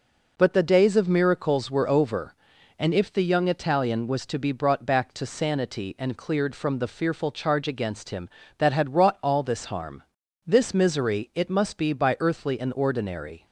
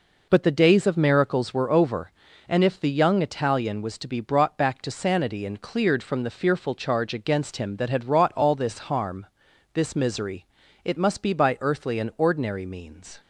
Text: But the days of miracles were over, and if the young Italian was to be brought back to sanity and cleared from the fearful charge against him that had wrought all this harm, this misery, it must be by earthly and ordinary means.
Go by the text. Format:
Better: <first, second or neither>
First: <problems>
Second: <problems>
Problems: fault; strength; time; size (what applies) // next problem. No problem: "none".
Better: second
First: stops before "means"; at 13.4 s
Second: none